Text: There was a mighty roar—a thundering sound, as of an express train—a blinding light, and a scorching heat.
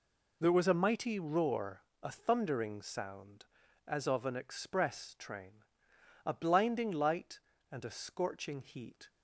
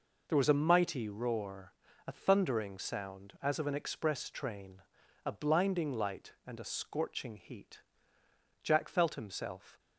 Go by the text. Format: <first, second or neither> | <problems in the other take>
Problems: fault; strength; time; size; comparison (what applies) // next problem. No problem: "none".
first | goes on to say "Jack felt himself"; noticeable; from 8.6 s on; 1.1 s long